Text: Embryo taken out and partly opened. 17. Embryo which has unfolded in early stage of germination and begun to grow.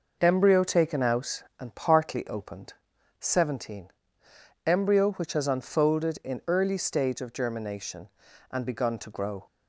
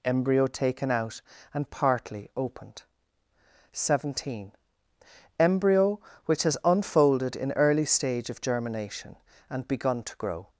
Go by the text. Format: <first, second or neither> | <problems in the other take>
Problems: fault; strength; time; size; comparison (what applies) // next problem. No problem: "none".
neither | none